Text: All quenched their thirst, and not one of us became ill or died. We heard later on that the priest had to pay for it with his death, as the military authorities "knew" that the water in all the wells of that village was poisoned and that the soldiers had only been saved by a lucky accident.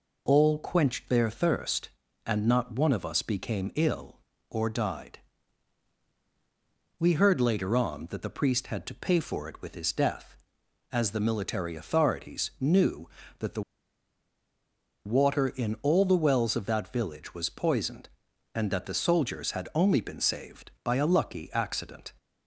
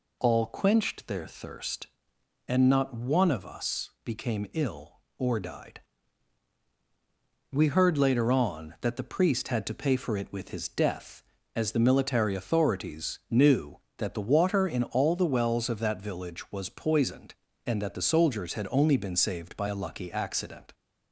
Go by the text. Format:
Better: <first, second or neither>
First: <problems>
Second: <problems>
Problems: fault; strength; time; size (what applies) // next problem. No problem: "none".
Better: second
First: pauses between "the" and "water"; strong; at 13.6 s; 1.4 s long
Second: none